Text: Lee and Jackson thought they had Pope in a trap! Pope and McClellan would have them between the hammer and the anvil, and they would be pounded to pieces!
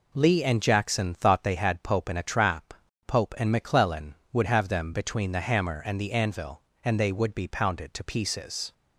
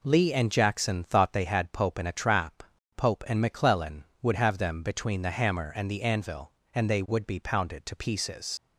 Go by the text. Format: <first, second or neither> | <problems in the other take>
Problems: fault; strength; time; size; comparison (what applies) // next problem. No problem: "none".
first | leaves "pieces" unfinished; at 8.5 s; 80 ms